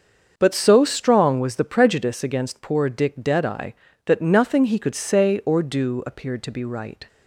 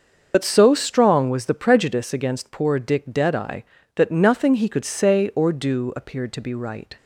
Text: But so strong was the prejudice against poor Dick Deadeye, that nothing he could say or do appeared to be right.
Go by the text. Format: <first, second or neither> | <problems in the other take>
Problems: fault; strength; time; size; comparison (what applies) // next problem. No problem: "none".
first | loses the start of "But"; at 0.3 s; 70 ms // starts louder than the rest; noticeable; until 1.3 s; 6 dB; also in the first